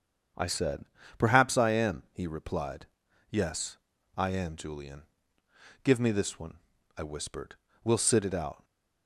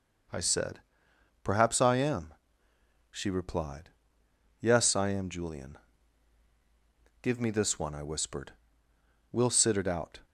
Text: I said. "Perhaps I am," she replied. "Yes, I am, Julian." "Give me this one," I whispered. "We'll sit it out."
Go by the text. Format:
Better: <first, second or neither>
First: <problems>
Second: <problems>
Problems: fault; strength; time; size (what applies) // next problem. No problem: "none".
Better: second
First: starts louder than the rest; strong; until 1.6 s; 7.5 dB // says "he" for "she"; at 2.1 s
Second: none